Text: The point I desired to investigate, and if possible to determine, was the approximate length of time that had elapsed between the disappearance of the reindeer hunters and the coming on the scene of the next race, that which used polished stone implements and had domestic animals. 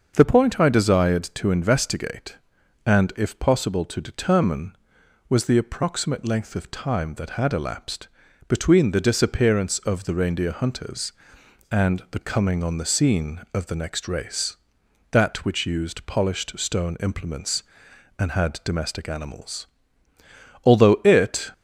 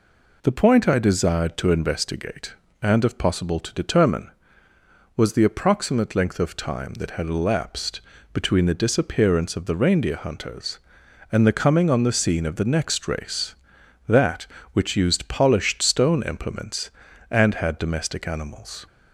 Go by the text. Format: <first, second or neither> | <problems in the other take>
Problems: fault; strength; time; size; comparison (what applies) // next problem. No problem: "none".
second | starts louder than the rest; until 1.1 s; 6.5 dB // pauses between "elapsed" and "between"; at 8.0 s; 0.40 s long; slight in the second // goes on to say "Although it"; noticeable; from 20.6 s on; 0.88 s long